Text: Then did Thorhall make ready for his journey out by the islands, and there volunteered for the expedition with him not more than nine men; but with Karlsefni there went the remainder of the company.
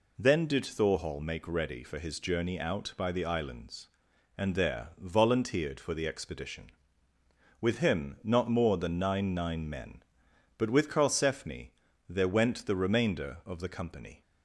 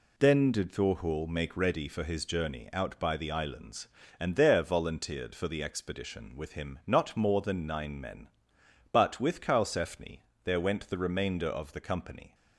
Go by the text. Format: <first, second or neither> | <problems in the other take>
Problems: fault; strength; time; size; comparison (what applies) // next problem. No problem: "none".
second | says "nine" twice; at 9.3 s // pauses between "Karlsefni" and "there"; slight; at 11.7 s; 0.36 s long; slight in the second